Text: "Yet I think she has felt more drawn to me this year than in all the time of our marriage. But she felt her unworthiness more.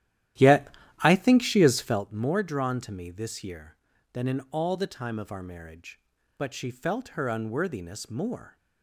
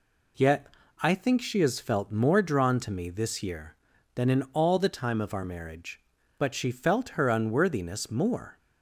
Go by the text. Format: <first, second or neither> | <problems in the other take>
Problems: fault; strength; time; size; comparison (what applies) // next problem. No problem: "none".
second | starts louder than the rest; strong; until 2.0 s; 12.5 dB // pauses between "Yet" and "I"; slight; at 0.6 s; 0.34 s long; slight in the second